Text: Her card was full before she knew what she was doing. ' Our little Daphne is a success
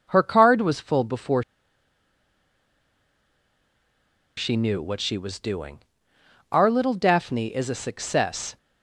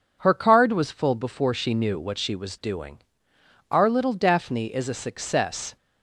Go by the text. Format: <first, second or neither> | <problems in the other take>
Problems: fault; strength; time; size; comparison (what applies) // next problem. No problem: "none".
second | pauses between "before" and "she"; strong; at 1.4 s; 2.9 s long